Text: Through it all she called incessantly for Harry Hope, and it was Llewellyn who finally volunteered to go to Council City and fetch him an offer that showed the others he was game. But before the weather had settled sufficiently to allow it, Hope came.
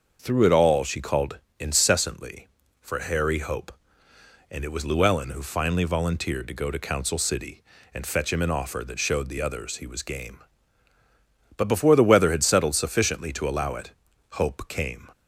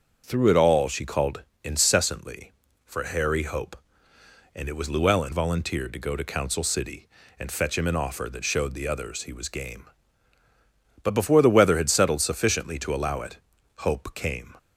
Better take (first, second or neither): first